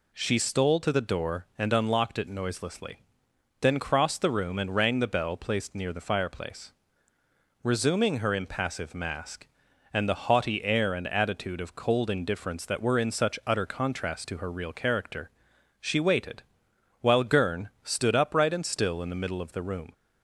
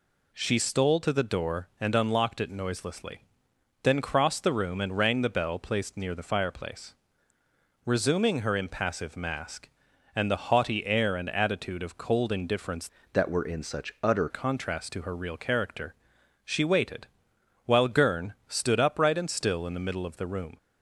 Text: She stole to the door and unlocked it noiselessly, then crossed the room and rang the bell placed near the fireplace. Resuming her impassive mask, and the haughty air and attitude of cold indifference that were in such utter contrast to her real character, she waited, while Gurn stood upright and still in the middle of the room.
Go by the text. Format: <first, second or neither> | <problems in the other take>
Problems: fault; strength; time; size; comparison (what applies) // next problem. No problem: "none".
first | changes voice from "that" to "utter"; from 13.1 to 14.2 s; 1.1 s long